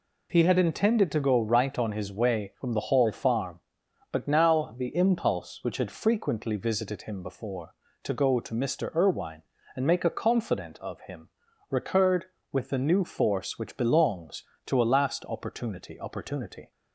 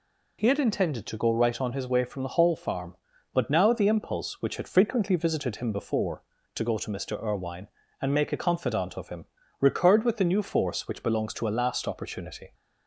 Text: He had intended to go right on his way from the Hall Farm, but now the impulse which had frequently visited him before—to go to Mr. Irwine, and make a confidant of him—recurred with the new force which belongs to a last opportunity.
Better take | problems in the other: second | says "opportunity" twice; at 15.9 s

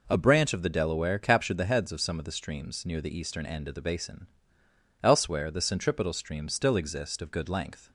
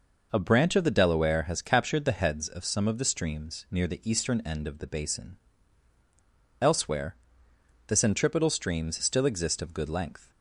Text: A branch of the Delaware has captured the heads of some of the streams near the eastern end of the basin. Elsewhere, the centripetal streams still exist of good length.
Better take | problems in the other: second | skips "has"; at 1.1 s

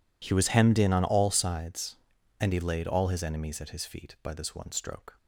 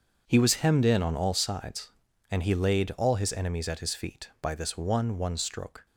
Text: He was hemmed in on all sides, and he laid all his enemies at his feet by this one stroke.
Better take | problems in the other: first | starts louder than the rest; until 1.2 s; 6.5 dB // says "one" twice; at 5.1 s

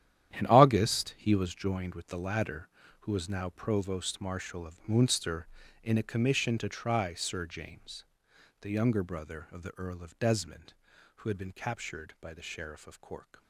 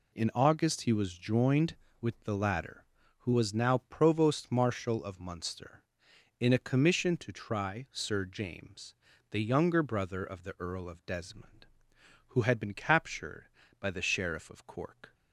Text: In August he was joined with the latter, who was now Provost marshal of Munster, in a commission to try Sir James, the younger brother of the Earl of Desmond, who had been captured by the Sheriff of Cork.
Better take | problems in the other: second | gets quieter; strong; throughout; 13.5 dB

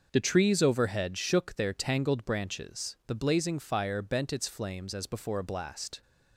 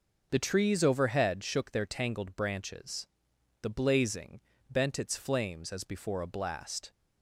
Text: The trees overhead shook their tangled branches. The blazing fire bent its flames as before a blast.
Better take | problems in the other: first | skips "fire"; at 4.5 s

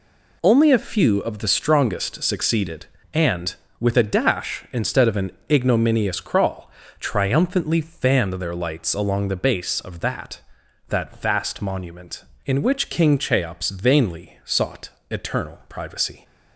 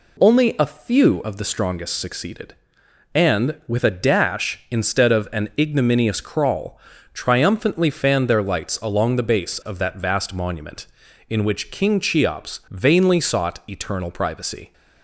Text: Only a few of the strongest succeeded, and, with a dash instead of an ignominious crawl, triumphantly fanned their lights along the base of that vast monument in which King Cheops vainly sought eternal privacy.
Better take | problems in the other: second | pauses between "an" and "ignominious"; slight; at 5.3 s; 0.18 s long // says "that" twice; at 10.8 s // pauses between "sought" and "eternal"; slight; at 14.8 s; 0.22 s long

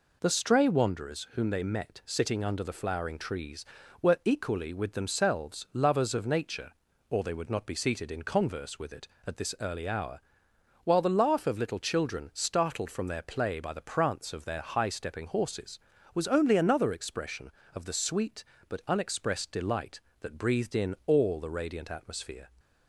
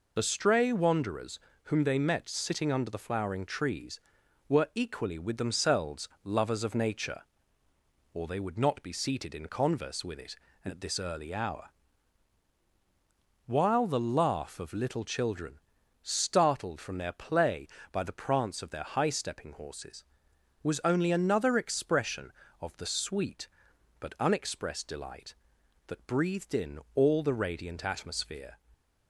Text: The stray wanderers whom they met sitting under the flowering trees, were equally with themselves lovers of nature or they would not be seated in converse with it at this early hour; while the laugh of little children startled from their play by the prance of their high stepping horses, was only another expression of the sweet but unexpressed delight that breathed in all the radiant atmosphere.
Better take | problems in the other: first | loses the start of "The"; at 0.1 s; 40 ms // pauses between "wanderers" and "whom"; slight; at 1.3 s; 0.26 s long // pauses between "themselves" and "lovers"; slight; at 6.0 s; 0.16 s long // pauses between "children" and "startled"; at 15.6 s; 0.42 s long // pauses between "in" and "all"; slight; at 26.8 s; 0.16 s long

